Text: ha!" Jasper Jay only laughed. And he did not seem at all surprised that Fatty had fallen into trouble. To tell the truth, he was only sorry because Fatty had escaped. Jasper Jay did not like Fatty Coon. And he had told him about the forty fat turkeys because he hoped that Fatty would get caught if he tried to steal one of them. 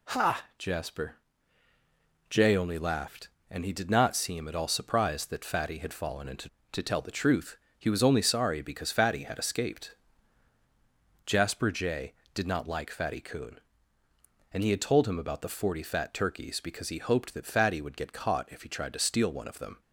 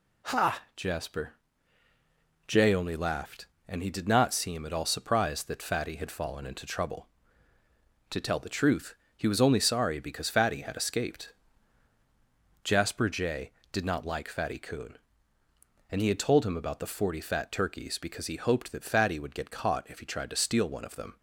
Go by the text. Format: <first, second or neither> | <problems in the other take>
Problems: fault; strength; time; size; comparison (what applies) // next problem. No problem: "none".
second | pauses between "Jasper" and "Jay"; at 1.1 s; 1.1 s long; also in the second // skips "trouble"; at 6.5 s